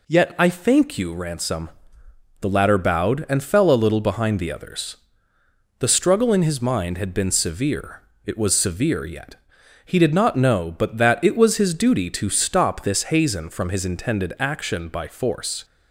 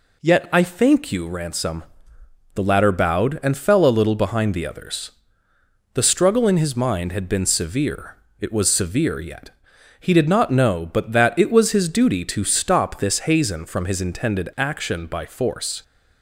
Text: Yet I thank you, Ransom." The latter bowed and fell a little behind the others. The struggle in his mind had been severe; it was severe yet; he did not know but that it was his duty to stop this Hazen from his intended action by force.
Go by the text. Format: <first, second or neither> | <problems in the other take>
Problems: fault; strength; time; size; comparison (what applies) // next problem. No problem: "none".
neither | none